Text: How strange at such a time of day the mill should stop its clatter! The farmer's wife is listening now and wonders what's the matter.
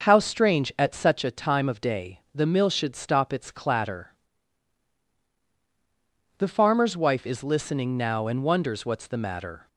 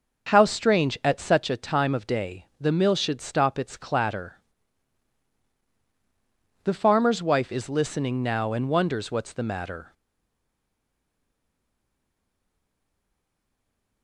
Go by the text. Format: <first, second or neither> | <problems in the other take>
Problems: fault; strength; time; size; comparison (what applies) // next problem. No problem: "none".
first | starts louder than the rest; until 1.3 s; 6.5 dB; also in the first // stays silent after the last word; strong; from 9.9 s on; 4.1 s long